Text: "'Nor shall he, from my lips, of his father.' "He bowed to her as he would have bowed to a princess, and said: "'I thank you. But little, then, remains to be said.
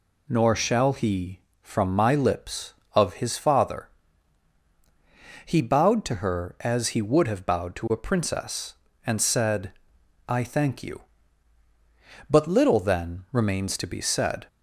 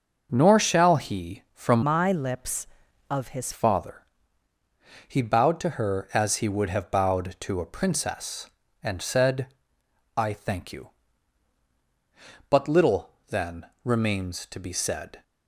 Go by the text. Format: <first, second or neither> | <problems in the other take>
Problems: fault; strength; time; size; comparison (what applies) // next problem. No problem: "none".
first | changes voice from "my" to "his"; from 1.8 to 3.5 s; 1.7 s long